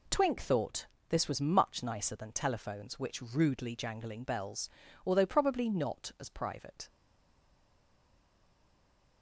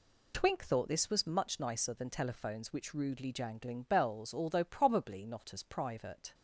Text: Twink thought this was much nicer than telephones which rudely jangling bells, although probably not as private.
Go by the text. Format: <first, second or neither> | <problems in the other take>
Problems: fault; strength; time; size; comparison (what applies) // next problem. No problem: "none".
second | pauses between "thought" and "this"; slight; at 0.8 s; 0.22 s long // stays silent after the last word; from 6.8 s on; 2.4 s long